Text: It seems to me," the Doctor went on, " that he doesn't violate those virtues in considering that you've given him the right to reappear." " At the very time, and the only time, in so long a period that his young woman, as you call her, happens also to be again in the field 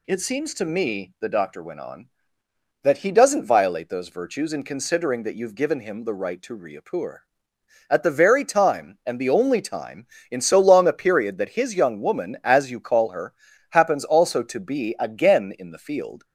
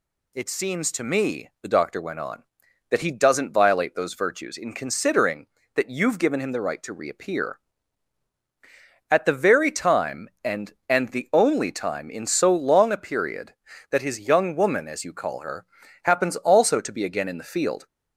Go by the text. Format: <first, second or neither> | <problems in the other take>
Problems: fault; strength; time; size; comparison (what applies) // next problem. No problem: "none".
first | says "and" twice; at 10.8 s